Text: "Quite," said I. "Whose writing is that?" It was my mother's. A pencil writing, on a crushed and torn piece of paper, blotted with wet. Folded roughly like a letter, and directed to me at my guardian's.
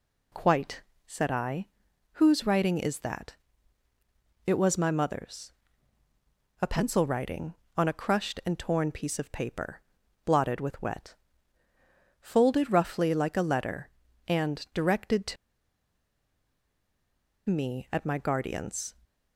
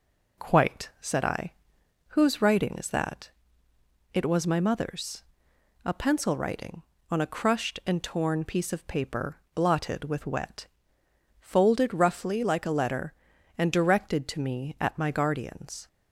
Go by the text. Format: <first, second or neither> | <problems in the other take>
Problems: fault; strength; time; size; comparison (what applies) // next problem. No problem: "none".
second | pauses between "to" and "me"; strong; at 15.3 s; 2.1 s long